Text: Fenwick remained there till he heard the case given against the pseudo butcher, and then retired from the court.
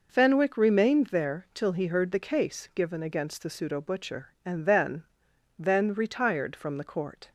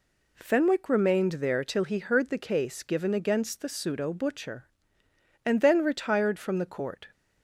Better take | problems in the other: second | says "then" twice; at 5.5 s

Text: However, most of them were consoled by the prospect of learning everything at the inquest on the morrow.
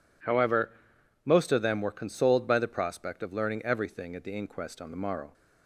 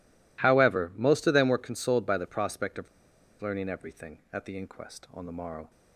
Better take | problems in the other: first | pauses between "of" and "learning"; noticeable; at 2.8 s; 0.53 s long

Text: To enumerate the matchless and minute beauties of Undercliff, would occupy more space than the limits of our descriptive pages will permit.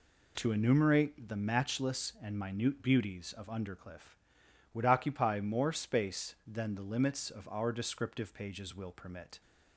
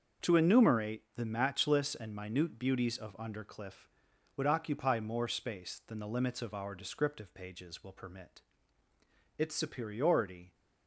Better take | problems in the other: first | starts louder than the rest; until 1.3 s; 6.5 dB // goes on to say "Its superiority"; noticeable; from 9.3 s on; 1.1 s long

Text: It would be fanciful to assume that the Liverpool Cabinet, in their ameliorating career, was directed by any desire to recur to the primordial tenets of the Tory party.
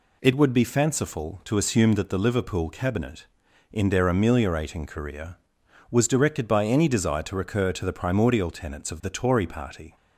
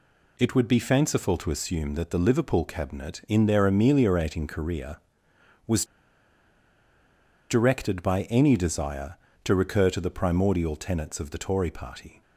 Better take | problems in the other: first | pauses between "was" and "directed"; strong; at 5.8 s; 1.6 s long

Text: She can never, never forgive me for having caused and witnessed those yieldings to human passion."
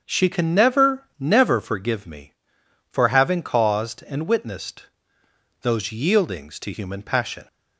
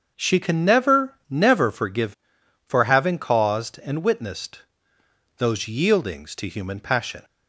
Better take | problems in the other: first | starts louder than the rest; until 1.1 s; 6.5 dB; also in the first // skips "me"; at 2.4 s // pauses between "witnessed" and "those"; noticeable; at 4.6 s; 0.76 s long; noticeable in the first

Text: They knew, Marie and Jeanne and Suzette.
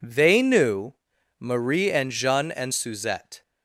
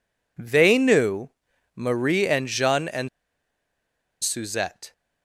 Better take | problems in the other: first | pauses between "and" and "Suzette"; at 3.0 s; 1.1 s long

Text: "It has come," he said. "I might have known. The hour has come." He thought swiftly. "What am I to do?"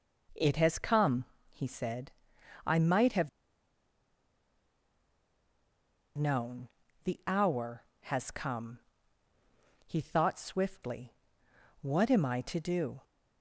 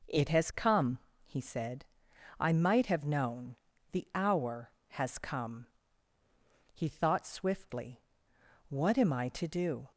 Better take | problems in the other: second | pauses between "have" and "known"; strong; at 3.2 s; 2.8 s long

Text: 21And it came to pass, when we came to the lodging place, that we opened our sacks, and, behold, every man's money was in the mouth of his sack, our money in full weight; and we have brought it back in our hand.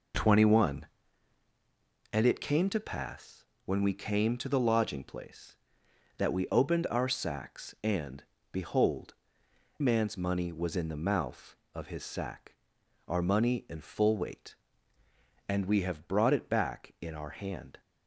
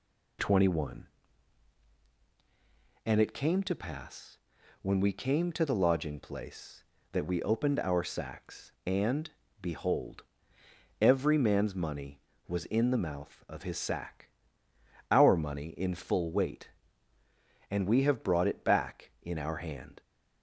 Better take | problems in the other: second | skips "every"; at 9.4 s

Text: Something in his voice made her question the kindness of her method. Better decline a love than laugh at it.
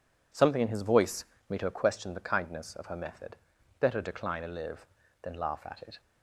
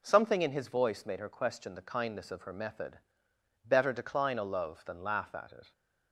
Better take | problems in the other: second | pauses between "voice" and "made"; slight; at 1.2 s; 0.24 s long // says "live" for "love"; at 4.4 s

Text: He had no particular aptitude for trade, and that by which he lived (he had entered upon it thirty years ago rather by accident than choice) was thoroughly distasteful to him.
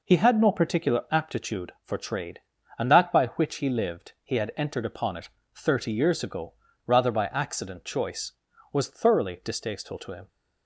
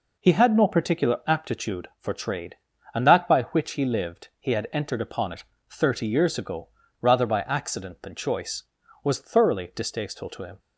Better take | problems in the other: second | pauses between "it" and "thirty"; slight; at 5.2 s; 0.26 s long; slight in the second // pauses between "ago" and "rather"; slight; at 6.5 s; 0.34 s long; slight in the second // skips "than"; at 7.8 s

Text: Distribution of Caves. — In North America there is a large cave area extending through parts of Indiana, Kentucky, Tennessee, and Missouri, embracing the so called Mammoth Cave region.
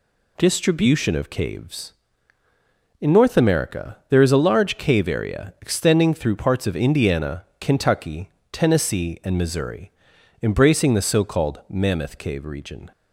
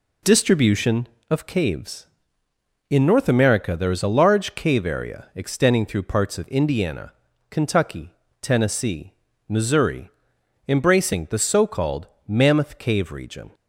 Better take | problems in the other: first | skips "and"; at 9.3 s // pauses between "called" and "Mammoth"; slight; at 12.0 s; 0.18 s long

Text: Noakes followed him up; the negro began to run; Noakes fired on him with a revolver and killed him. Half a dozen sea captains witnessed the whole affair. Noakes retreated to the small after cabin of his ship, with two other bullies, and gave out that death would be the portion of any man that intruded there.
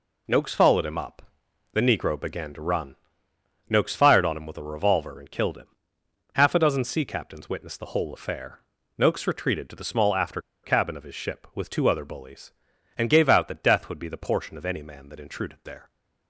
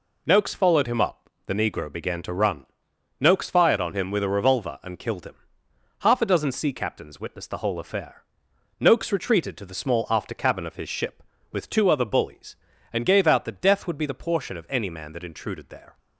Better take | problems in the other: second | pauses between "after" and "cabin"; slight; at 10.3 s; 0.24 s long

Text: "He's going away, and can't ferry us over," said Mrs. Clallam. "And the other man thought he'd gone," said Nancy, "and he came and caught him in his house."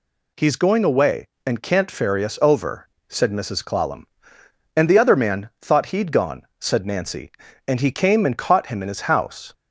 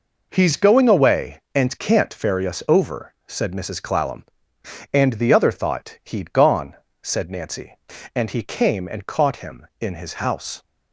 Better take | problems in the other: first | skips "man"; at 5.5 s

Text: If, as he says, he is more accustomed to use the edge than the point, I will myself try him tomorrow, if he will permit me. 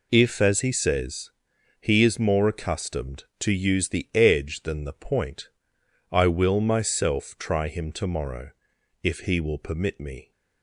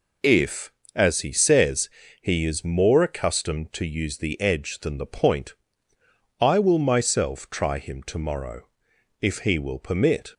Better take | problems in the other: first | stops before "me"; at 10.3 s

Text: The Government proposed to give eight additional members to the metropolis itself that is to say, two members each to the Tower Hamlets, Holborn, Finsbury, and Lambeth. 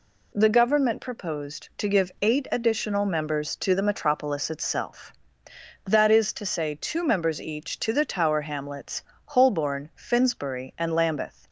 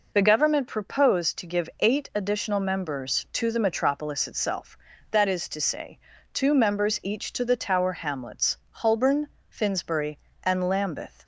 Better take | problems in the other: neither | none

